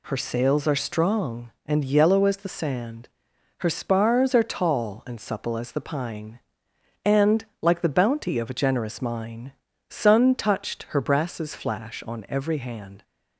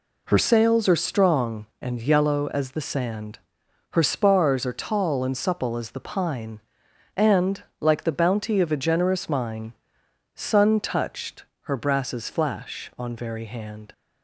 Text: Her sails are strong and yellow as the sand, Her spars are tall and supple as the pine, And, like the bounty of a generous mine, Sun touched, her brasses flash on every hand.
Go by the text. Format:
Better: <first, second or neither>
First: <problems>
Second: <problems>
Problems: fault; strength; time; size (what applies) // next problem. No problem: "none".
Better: first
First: none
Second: says "very" for "every"; at 13.1 s